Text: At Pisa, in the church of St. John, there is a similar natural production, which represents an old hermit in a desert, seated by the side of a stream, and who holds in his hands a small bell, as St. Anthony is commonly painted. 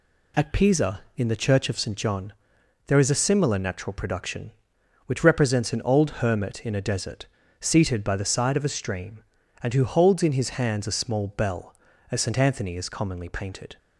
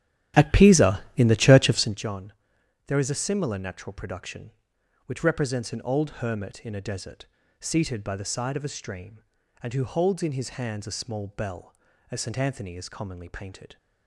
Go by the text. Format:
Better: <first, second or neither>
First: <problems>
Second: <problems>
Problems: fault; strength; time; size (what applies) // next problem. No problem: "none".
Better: first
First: none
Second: starts louder than the rest; strong; until 2.1 s; 11.5 dB